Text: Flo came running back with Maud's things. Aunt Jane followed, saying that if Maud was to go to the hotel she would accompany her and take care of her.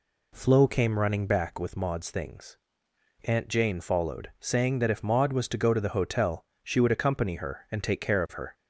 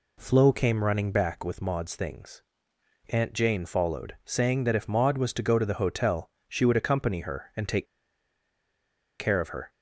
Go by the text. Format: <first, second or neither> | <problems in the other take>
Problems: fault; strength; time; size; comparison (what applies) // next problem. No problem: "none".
first | pauses between "hotel" and "she"; slight; at 6.2 s; 0.22 s long; slight in the first // pauses between "take" and "care"; strong; at 7.8 s; 1.3 s long